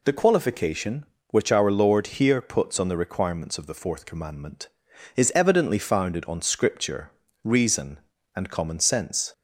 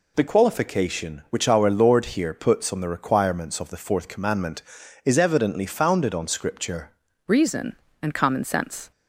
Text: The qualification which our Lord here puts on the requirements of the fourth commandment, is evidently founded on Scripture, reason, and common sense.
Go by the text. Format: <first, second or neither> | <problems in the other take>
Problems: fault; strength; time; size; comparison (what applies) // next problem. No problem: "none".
first | changes voice at "reason"; from 7.2 s on; 1.7 s long